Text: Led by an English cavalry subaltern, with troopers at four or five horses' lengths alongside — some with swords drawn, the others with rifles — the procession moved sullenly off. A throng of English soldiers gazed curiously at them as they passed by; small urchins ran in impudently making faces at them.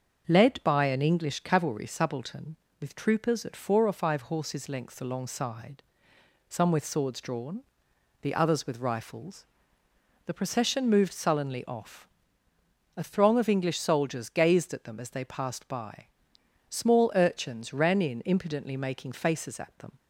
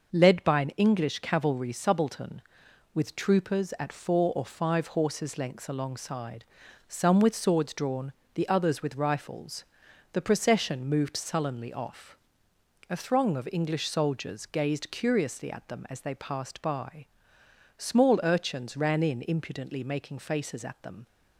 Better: second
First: starts louder than the rest; until 1.2 s; 6.5 dB // skips "curiously"; at 14.7 s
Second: none

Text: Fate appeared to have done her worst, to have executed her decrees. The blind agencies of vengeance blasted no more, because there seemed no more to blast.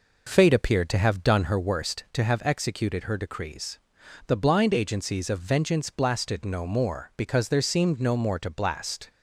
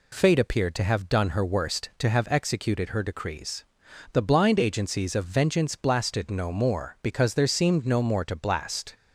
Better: second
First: starts louder than the rest; noticeable; until 1.7 s; 4.5 dB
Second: none

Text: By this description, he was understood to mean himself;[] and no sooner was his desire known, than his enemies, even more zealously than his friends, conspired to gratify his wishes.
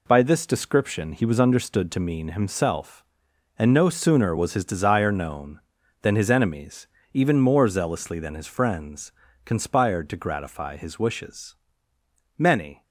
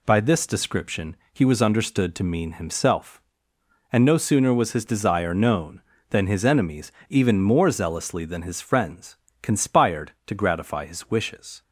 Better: second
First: goes on to say "Many"; slight; from 12.3 s on; 0.46 s long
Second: none

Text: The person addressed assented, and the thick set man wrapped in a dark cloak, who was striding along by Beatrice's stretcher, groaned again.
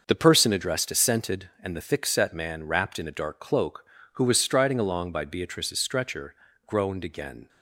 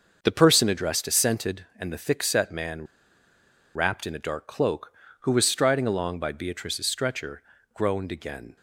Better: first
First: starts louder than the rest; until 1.0 s; 6 dB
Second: starts louder than the rest; until 1.2 s; 6 dB // pauses between "man" and "wrapped"; noticeable; at 2.8 s; 0.90 s long

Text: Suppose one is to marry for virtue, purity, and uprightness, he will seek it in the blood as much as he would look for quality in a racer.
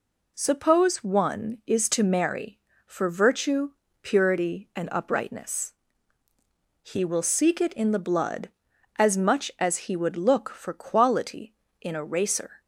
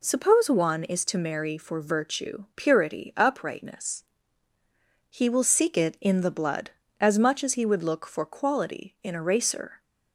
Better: first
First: none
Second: skips "and"; at 3.1 s

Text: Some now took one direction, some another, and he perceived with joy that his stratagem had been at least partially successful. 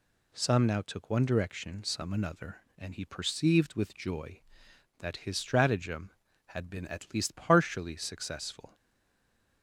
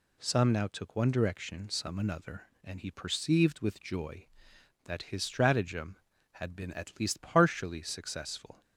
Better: second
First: stays silent after the last word; slight; from 8.7 s on; 0.9 s long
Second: none

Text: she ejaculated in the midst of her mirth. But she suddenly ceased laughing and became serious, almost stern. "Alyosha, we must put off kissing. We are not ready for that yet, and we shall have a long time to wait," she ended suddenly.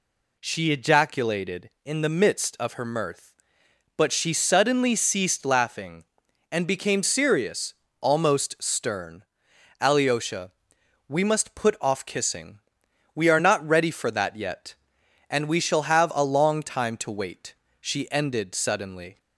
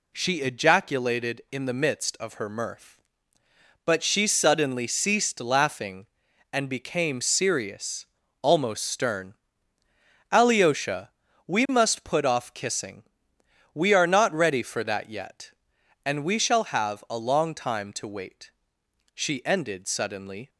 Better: neither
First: none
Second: none

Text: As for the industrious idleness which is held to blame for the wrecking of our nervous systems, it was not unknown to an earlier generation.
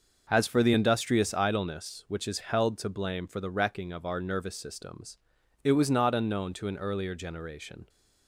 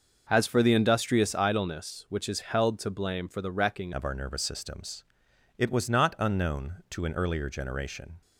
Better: first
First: starts louder than the rest; noticeable; until 1.3 s; 6 dB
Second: starts louder than the rest; noticeable; until 1.3 s; 6 dB // changes voice at "of"; from 3.9 s on; 4.3 s long

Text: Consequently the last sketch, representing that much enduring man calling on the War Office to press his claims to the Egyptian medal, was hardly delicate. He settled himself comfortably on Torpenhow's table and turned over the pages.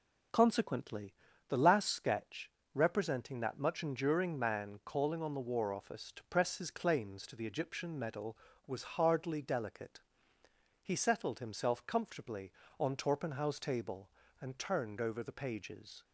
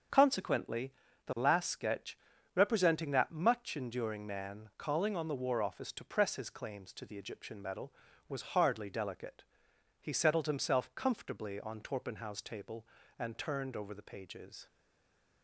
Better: first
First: pauses between "Consequently" and "the"; slight; at 1.1 s; 0.36 s long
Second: starts louder than the rest; strong; until 1.5 s; 7.5 dB // pauses between "Consequently" and "the"; slight; at 0.9 s; 0.36 s long // stays silent after the last word; slight; from 14.6 s on; 0.8 s long

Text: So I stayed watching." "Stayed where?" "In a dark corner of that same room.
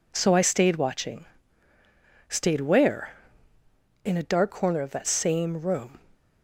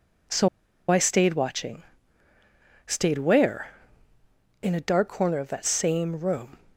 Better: first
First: none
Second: pauses between "So" and "I"; at 0.4 s; 0.41 s long

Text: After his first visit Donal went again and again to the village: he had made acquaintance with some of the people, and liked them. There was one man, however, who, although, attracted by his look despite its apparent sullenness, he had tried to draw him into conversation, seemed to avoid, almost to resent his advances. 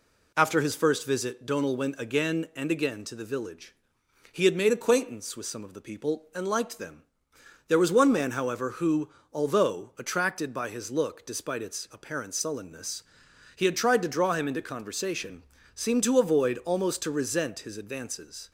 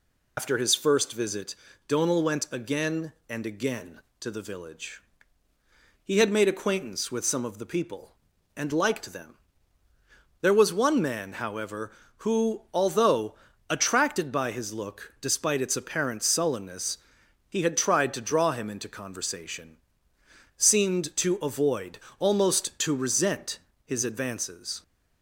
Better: first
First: none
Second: loses the start of "After"; at 0.3 s; 105 ms // pauses between "visit" and "Donal"; slight; at 1.5 s; 0.32 s long // pauses between "resent" and "his"; slight; at 23.5 s; 0.26 s long

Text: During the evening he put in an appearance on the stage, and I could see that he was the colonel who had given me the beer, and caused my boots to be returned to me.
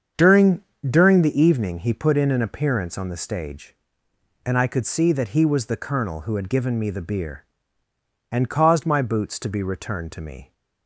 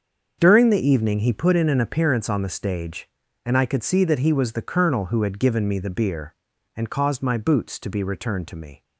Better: second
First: starts louder than the rest; until 1.4 s; 7 dB // says "During" twice; at 0.8 s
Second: starts louder than the rest; until 1.4 s; 6.5 dB

